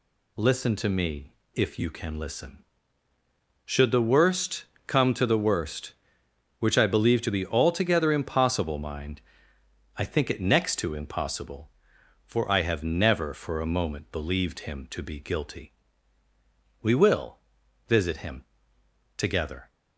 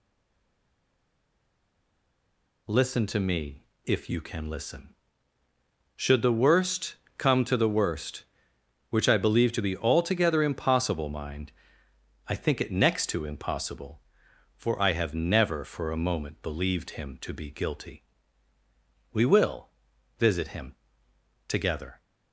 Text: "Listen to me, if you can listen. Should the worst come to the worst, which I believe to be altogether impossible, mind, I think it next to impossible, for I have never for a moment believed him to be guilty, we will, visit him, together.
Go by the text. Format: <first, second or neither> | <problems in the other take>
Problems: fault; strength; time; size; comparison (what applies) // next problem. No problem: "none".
first | stays silent before the first word; strong; until 2.6 s; 2.6 s long // pauses between "worst" and "come"; slight; at 6.9 s; 0.24 s long; slight in the first